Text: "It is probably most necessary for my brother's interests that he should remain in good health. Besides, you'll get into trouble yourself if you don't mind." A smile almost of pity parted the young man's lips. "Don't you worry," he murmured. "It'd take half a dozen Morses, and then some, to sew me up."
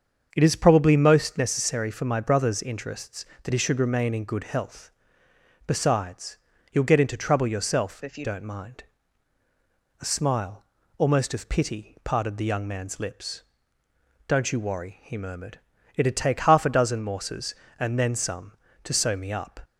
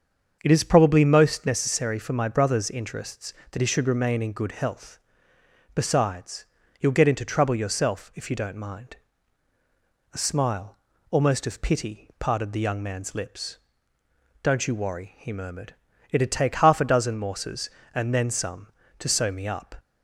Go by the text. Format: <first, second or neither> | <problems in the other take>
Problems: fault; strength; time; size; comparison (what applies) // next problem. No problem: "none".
second | starts louder than the rest; until 1.3 s; 7 dB; also in the second // changes voice from "if" to "you"; from 8.0 to 8.2 s; 0.2 s long // pauses between "smile" and "almost"; slight; at 10.6 s; 0.34 s long; slight in the second